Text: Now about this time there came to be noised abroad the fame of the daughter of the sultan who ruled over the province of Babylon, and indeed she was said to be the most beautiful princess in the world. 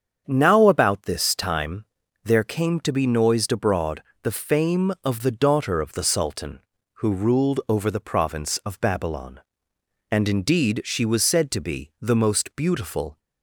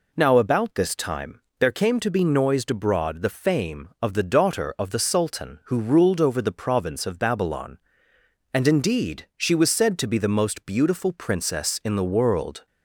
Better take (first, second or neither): second